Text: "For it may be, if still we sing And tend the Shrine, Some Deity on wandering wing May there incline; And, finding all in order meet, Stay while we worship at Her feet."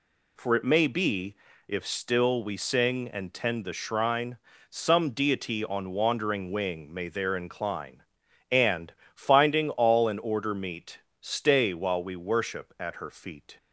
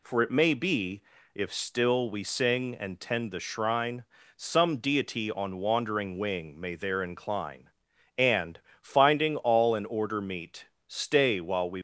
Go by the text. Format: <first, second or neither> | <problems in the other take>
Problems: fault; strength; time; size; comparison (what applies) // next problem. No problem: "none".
first | stops before "worship at Her feet"; at 11.7 s